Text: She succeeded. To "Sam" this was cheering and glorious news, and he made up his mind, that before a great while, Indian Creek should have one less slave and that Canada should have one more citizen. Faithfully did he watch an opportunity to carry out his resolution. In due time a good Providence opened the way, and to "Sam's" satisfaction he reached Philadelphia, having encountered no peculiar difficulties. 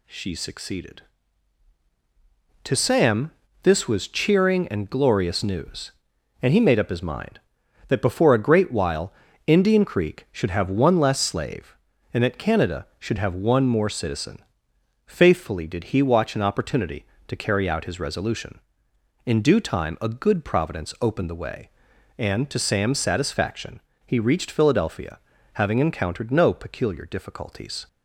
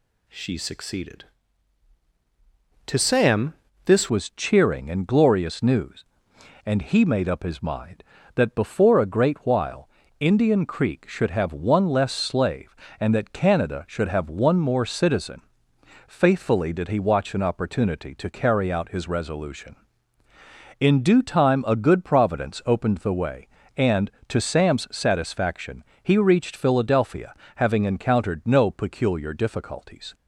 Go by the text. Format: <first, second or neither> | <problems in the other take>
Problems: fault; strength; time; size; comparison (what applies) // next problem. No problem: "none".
first | pauses between "Sam" and "this"; slight; at 3.5 s; 0.32 s long; slight in the first // changes voice at "was"; from 4.0 s on; 26.1 s long // pauses between "satisfaction" and "he"; slight; at 25.8 s; 0.18 s long; slight in the first